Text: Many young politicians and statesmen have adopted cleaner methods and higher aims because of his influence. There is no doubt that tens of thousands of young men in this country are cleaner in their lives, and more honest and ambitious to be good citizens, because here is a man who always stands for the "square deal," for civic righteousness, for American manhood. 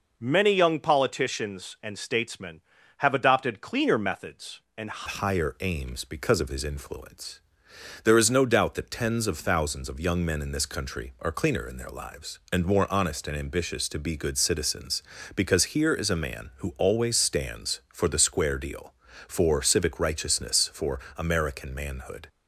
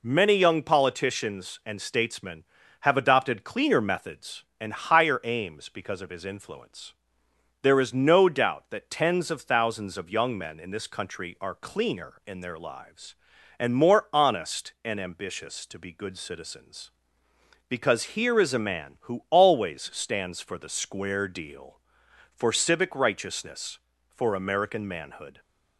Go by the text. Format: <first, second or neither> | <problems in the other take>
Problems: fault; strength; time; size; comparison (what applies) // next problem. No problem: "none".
second | changes voice at "higher"; from 5.0 s on; 17.2 s long // pauses between "for" and "American"; slight; at 20.9 s; 0.20 s long